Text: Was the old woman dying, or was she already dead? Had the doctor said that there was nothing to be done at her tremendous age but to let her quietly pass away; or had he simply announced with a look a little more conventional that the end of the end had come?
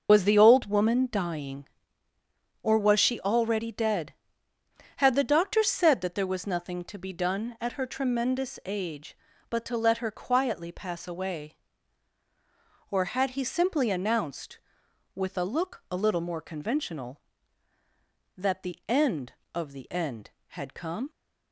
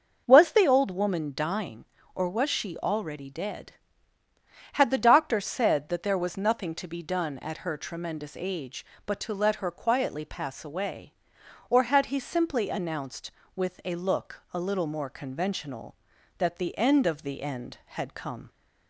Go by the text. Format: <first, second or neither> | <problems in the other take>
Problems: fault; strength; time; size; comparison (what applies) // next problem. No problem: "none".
second | loses the start of "Was"; at 0.0 s; 60 ms // starts louder than the rest; until 1.1 s; 6 dB; also in the second